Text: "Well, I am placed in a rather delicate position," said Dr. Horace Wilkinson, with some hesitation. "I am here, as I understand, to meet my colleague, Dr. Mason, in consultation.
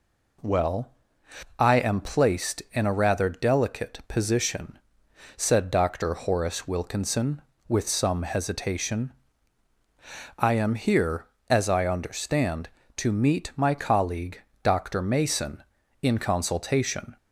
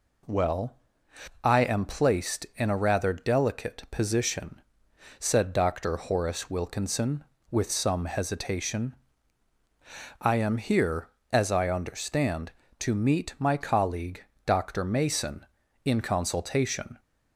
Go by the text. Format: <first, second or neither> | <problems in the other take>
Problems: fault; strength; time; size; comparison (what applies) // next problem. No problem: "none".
neither | none